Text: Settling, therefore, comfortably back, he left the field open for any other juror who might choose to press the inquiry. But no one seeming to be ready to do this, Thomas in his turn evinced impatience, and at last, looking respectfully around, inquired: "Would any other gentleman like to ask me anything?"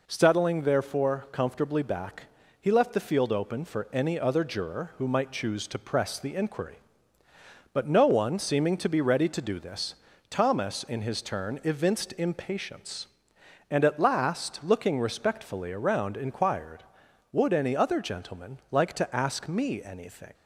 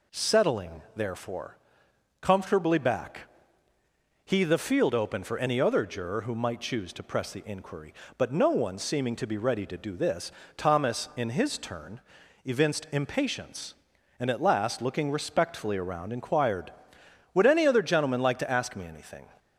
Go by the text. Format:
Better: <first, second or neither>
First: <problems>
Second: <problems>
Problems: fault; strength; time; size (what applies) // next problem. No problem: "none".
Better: first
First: none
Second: skips "left"; at 4.4 s // pauses between "turn" and "evinced"; at 12.0 s; 0.44 s long